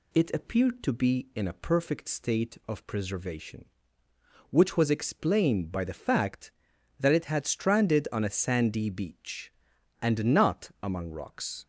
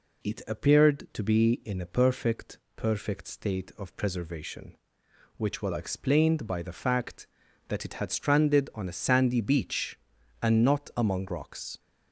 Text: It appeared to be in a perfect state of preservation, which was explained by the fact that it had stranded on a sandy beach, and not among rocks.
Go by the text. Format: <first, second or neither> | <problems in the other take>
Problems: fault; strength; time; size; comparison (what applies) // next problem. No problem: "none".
first | says "perfect" twice; at 2.7 s